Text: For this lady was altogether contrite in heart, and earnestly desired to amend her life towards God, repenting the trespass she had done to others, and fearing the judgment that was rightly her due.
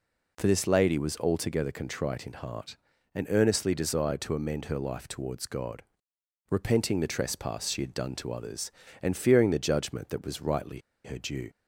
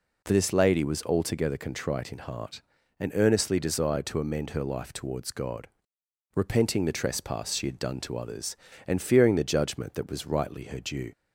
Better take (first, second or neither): second